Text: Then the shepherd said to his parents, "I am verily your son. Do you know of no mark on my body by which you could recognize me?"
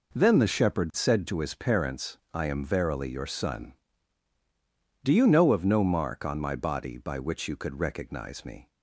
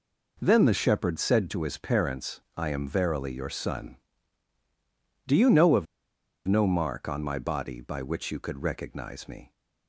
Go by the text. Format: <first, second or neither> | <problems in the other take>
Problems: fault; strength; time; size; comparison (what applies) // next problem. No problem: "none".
first | pauses between "of" and "no"; noticeable; at 5.8 s; 0.62 s long